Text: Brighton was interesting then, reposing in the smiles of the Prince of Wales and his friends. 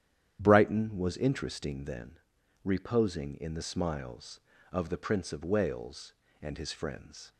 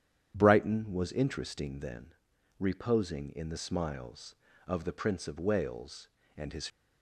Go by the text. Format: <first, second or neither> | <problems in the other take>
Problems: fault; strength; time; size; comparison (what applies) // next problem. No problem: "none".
first | starts louder than the rest; strong; until 1.3 s; 9.5 dB; strong in the first // stops before "friends"; at 6.6 s